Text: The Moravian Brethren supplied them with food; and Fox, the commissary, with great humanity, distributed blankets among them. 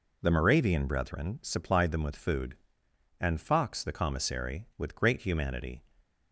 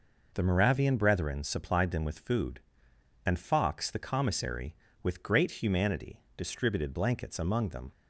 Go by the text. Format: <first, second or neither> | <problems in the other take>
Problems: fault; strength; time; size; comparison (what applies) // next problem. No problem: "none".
second | stops before "distributed blankets among them"; at 6.0 s